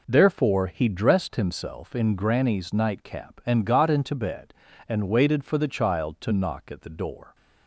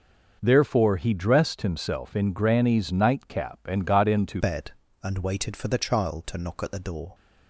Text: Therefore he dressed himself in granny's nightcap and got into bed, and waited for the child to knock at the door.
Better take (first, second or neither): first